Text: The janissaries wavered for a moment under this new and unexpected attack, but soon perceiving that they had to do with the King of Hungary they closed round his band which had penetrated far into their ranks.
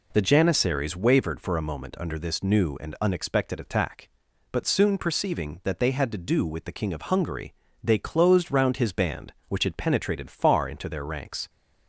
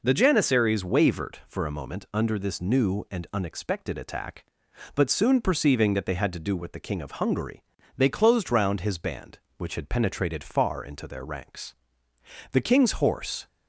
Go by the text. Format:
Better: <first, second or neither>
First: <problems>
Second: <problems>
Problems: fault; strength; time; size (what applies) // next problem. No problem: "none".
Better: first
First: pauses between "Hungary" and "they"; slight; at 7.5 s; 0.30 s long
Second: pauses between "Hungary" and "they"; slight; at 7.6 s; 0.34 s long // goes on to say "The king's horse"; noticeable; from 12.5 s on; 0.96 s long